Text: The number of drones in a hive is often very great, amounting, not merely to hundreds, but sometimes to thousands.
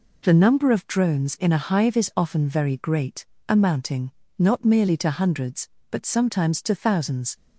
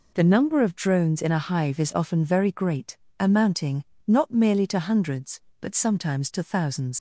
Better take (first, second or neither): first